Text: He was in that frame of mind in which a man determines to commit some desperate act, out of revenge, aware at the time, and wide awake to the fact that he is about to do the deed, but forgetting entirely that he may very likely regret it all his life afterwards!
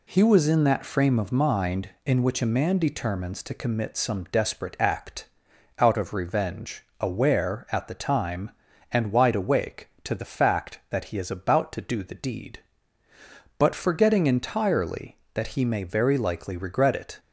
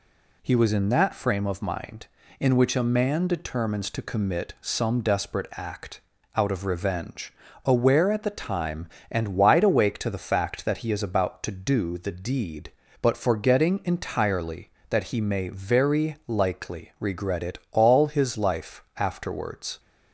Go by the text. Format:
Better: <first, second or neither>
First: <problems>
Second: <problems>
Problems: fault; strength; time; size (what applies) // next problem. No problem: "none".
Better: second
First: stops before "all his life afterwards"; at 17.1 s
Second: none